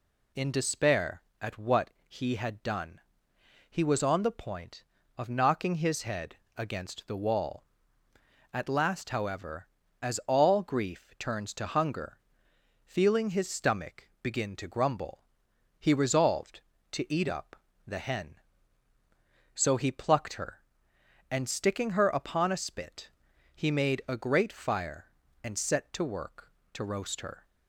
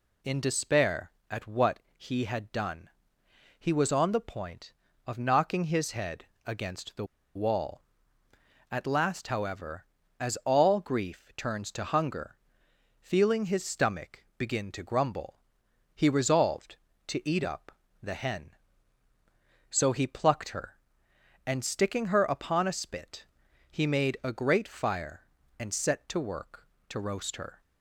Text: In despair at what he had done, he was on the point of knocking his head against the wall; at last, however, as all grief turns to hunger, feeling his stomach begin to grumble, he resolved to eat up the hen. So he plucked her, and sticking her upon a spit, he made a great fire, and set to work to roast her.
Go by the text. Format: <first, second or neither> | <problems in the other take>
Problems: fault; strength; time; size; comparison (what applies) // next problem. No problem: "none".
first | pauses between "what" and "he"; slight; at 1.7 s; 0.16 s long; slight in the first // pauses between "head" and "against"; slight; at 6.2 s; 0.20 s long; slight in the first // pauses between "the" and "wall"; slight; at 7.0 s; 0.29 s long // pauses between "up" and "the"; slight; at 17.7 s; 0.32 s long; slight in the first